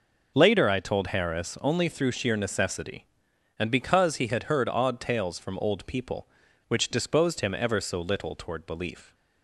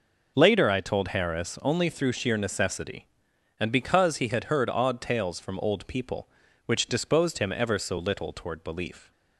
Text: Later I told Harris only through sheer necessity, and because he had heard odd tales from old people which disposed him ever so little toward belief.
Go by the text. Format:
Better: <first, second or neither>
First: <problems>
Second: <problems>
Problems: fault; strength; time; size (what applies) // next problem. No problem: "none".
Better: neither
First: none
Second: none